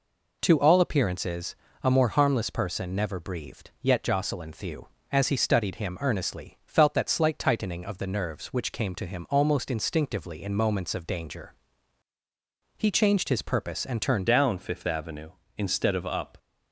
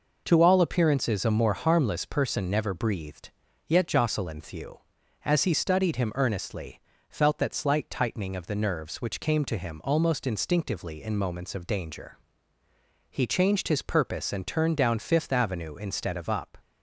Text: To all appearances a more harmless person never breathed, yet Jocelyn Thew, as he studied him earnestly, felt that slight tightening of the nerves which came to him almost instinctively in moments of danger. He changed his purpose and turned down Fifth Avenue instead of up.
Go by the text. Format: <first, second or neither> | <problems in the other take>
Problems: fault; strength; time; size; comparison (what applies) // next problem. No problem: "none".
second | pauses between "appearances" and "a"; slight; at 1.5 s; 0.28 s long // changes voice at "down"; from 14.2 s on; 2.1 s long